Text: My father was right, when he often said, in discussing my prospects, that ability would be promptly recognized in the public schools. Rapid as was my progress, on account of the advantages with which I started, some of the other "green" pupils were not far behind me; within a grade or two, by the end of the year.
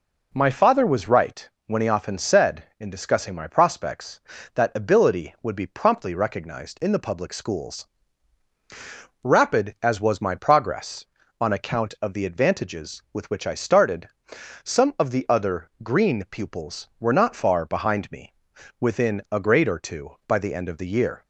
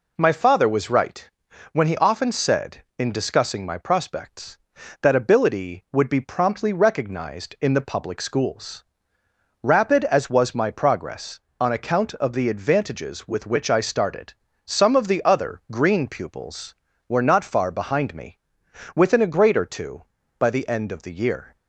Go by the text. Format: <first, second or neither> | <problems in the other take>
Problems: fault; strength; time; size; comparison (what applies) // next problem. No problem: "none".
neither | none